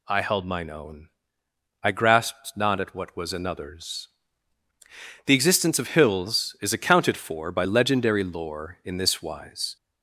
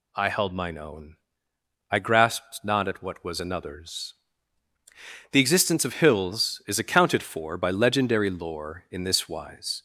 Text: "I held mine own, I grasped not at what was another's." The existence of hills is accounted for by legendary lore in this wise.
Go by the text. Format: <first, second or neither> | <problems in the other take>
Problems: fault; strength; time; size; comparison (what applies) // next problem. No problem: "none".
neither | none